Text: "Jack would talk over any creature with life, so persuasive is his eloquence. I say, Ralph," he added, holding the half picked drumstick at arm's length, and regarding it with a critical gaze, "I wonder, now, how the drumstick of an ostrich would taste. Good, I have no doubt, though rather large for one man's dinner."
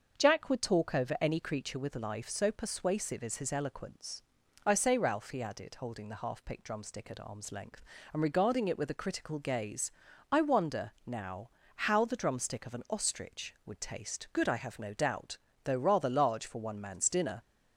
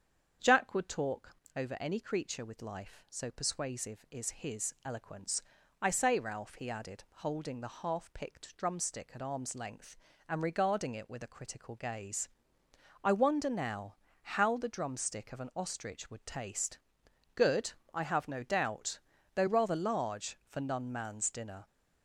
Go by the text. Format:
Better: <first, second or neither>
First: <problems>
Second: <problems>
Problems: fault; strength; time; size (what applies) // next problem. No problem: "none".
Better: first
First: starts louder than the rest; until 1.2 s; 6.5 dB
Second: starts louder than the rest; strong; until 1.5 s; 7.5 dB // pauses between "talk" and "over"; slight; at 1.3 s; 0.18 s long // says "none" for "one"; at 20.6 s